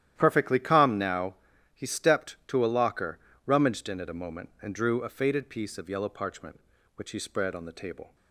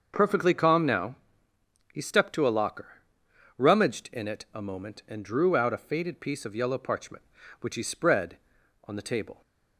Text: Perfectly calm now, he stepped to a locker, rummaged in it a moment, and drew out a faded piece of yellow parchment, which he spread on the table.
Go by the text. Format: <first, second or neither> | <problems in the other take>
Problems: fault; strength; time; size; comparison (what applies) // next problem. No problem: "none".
second | starts louder than the rest; strong; until 1.1 s; 11.5 dB; also in the second // skips "out"; at 5.0 s